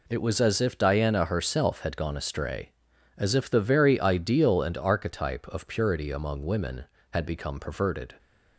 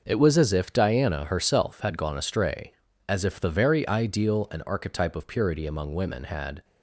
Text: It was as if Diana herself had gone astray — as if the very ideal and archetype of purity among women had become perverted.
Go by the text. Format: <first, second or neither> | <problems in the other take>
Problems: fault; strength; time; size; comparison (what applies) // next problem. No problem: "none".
first | stops before "become perverted"; at 6.6 s